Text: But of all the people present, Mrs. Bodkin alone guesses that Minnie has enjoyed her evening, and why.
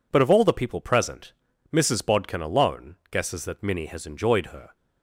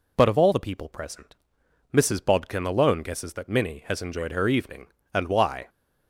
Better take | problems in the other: second | stops before "evening and why"; at 4.7 s

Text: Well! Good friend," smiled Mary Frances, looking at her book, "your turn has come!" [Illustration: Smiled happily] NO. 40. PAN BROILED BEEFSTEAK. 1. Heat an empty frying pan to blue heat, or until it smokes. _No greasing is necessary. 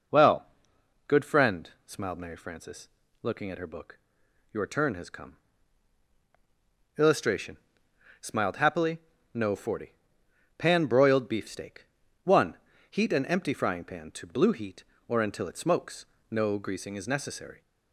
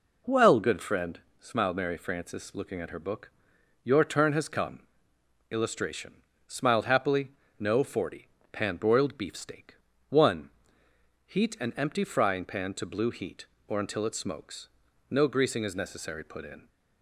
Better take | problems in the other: first | pauses between "happily" and "NO"; slight; at 7.3 s; 0.26 s long; slight in the first // goes on to say "Put in"; slight; from 16.2 s on; 0.44 s long

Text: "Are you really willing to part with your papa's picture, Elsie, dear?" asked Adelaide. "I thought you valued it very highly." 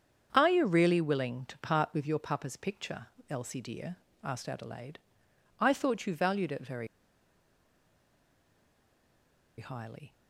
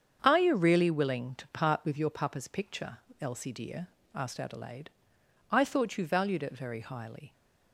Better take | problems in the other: second | starts louder than the rest; strong; until 1.3 s; 7.5 dB; strong in the second // pauses between "very" and "highly"; strong; at 6.8 s; 2.7 s long

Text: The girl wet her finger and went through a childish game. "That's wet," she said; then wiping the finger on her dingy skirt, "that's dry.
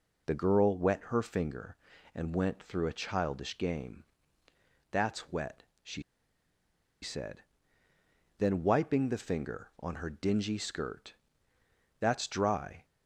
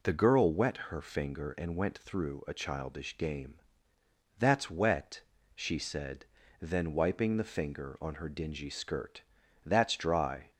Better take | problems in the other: second | pauses between "she" and "said"; at 6.0 s; 1.0 s long

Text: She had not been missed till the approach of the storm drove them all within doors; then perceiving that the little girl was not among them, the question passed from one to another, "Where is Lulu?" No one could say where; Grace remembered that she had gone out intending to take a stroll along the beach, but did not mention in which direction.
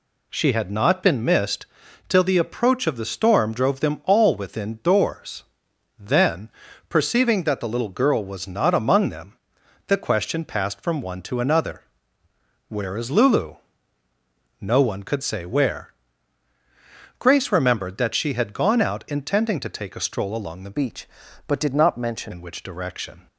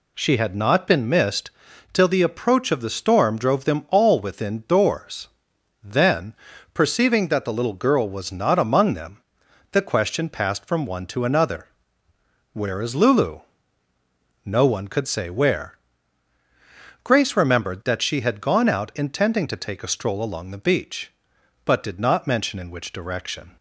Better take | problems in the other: second | pauses between "missed" and "till"; at 1.6 s; 0.40 s long; also in the second // pauses between "then" and "perceiving"; at 6.4 s; 0.40 s long; also in the second // changes voice from "beach" to "mention"; from 20.7 to 22.3 s; 1.6 s long

